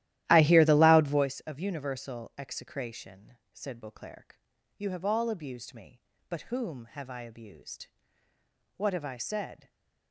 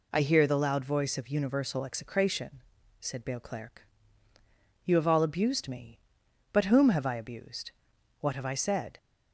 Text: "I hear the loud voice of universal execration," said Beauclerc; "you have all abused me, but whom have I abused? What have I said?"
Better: second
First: starts louder than the rest; strong; until 1.3 s; 14 dB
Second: none

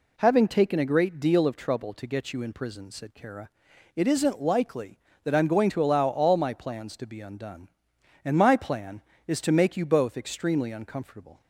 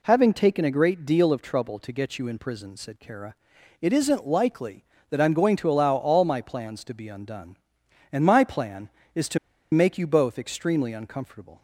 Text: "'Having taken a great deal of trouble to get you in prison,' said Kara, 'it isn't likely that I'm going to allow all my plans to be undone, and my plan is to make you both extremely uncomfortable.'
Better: first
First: none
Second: pauses between "to" and "make"; slight; at 9.3 s; 0.35 s long

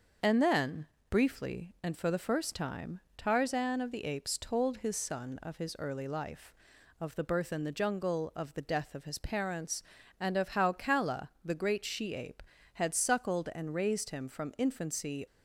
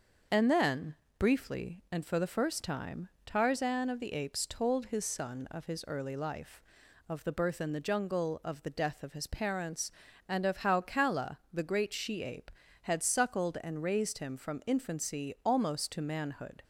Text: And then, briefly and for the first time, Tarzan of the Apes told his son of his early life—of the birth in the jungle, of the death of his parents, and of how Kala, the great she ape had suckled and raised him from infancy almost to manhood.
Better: second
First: starts louder than the rest; until 1.4 s; 6.5 dB // stops before "almost to manhood"; at 15.2 s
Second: starts louder than the rest; until 1.5 s; 6.5 dB

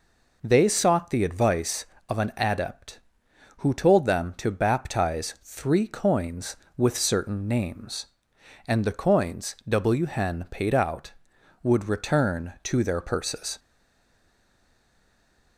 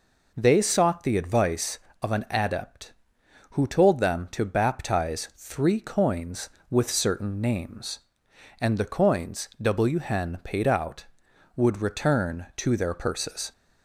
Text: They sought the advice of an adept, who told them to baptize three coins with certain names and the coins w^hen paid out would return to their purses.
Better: second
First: stays silent after the last word; noticeable; from 13.5 s on; 2.0 s long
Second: none

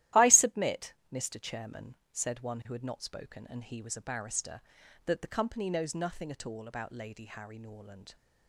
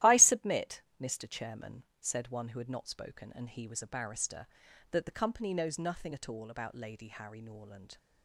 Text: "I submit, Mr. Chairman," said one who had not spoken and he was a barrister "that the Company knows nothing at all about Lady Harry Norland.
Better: neither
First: starts louder than the rest; strong; until 1.3 s; 14.5 dB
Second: starts louder than the rest; strong; until 1.2 s; 14 dB

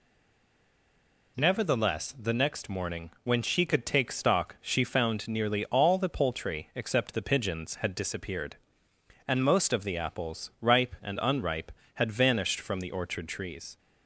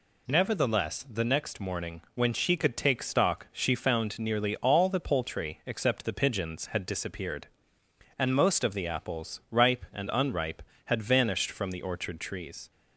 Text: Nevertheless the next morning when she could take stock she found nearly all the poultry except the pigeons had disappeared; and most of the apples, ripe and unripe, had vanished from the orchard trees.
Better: second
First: stays silent before the first word; noticeable; until 1.3 s; 1.3 s long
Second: none

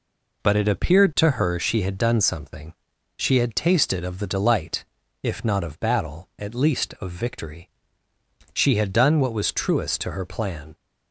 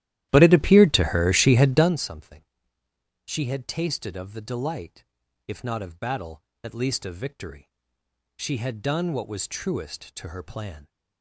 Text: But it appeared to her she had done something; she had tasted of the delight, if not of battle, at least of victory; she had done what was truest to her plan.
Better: first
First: none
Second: starts louder than the rest; strong; until 2.0 s; 13.5 dB

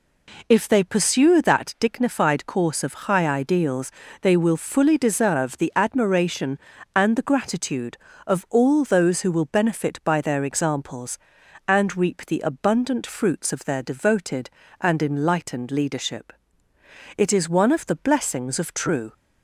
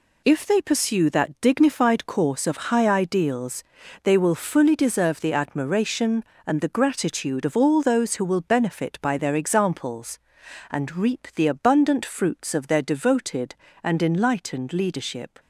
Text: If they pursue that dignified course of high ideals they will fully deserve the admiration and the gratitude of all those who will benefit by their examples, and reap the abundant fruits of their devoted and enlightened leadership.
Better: second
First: pauses between "ideals" and "they"; slight; at 3.9 s; 0.30 s long // goes on to say "It is one of the blessings of true"; strong; from 17.1 s on; 1.9 s long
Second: pauses between "ideals" and "they"; at 3.6 s; 0.40 s long

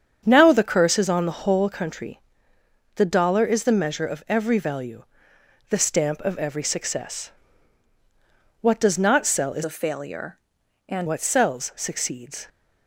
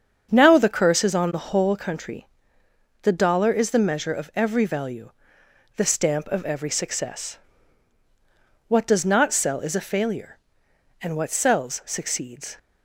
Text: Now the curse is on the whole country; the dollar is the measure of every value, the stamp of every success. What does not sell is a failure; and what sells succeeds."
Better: second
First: starts louder than the rest; strong; until 1.2 s; 7 dB // changes voice from "a" to "and"; from 9.6 to 11.0 s; 1.4 s long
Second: starts louder than the rest; strong; until 1.3 s; 7 dB

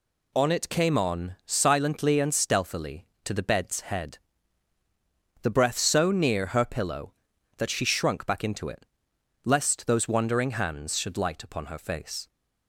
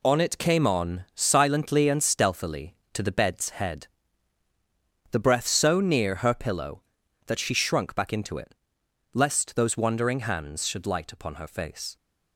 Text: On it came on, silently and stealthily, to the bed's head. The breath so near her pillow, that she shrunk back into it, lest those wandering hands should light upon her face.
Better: first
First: none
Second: gets quieter; strong; throughout; 8.5 dB

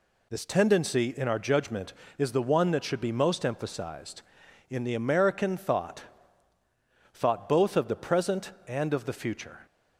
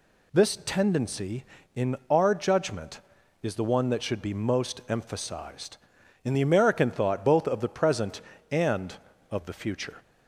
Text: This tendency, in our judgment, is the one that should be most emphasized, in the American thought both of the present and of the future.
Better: second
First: says "thought" twice; at 7.1 s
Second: none

